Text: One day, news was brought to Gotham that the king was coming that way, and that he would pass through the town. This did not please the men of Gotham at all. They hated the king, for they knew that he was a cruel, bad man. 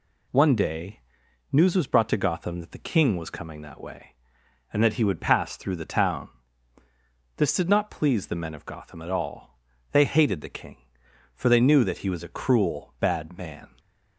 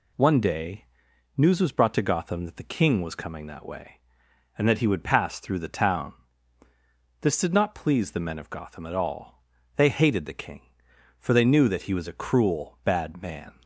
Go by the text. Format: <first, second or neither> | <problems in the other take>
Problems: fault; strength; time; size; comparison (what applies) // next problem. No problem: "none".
neither | none